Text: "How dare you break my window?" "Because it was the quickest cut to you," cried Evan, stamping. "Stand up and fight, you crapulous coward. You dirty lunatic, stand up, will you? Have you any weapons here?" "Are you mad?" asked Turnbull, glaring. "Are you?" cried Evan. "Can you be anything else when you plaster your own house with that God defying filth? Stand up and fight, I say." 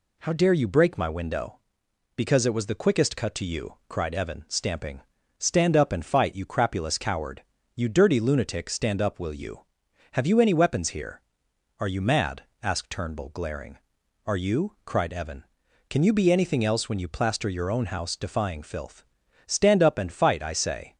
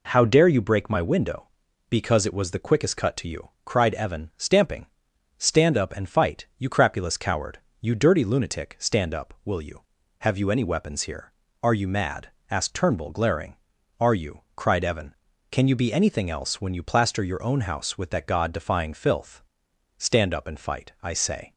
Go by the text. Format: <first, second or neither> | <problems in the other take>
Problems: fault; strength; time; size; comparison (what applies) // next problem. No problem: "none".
second | skips "with that God"; at 18.1 s